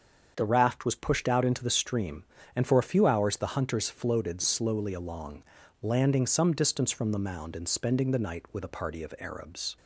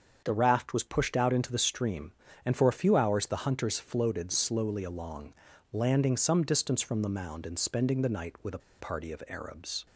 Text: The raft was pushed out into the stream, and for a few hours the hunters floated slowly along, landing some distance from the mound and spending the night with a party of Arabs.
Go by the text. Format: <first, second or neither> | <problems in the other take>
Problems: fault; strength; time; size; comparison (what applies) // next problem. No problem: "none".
first | starts louder than the rest; until 1.2 s; 6.5 dB; also in the first // pauses between "a" and "party"; slight; at 8.5 s; 0.20 s long